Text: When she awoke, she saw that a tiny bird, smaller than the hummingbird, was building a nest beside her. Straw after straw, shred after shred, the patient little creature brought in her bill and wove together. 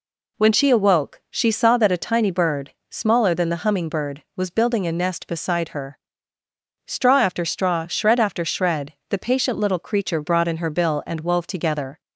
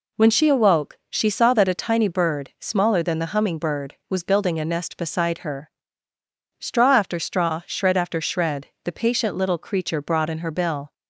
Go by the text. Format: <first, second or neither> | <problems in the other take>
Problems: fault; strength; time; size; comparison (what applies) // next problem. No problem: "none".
first | stops before "and wove together"; at 10.9 s